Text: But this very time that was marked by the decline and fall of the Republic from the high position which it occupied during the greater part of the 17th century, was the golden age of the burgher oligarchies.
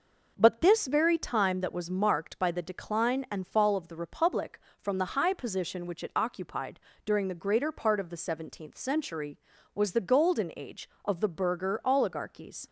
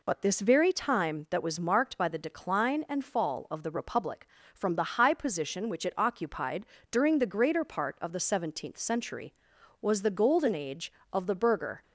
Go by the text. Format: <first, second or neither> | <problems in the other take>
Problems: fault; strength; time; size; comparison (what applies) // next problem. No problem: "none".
first | pauses between "occupied" and "during"; slight; at 6.6 s; 0.24 s long; slight in the first // stops before "oligarchies"; at 11.8 s